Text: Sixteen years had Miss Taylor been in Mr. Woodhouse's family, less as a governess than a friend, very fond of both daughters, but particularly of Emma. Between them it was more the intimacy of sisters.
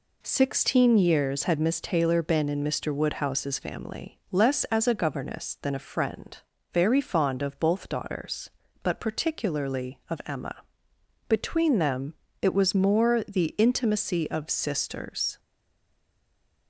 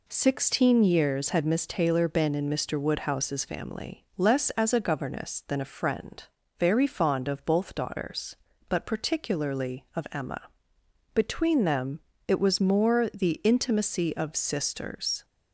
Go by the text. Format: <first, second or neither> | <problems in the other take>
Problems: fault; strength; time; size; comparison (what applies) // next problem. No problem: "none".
second | pauses between "them" and "it"; slight; at 12.1 s; 0.30 s long; slight in the second // stays silent after the last word; noticeable; from 15.3 s on; 1.3 s long